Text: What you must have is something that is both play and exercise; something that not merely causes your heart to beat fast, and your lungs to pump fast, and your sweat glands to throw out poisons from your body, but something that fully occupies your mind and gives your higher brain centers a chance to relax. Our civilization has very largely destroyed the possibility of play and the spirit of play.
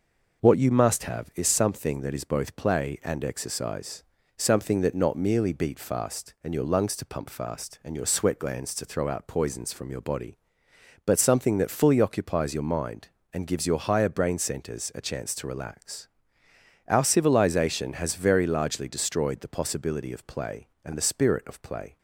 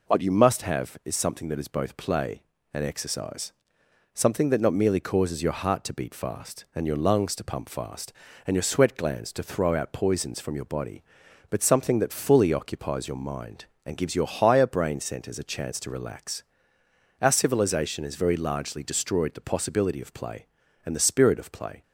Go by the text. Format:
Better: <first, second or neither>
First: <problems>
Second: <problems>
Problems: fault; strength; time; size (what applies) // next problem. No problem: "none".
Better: second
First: skips "causes your heart to"; at 5.5 s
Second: none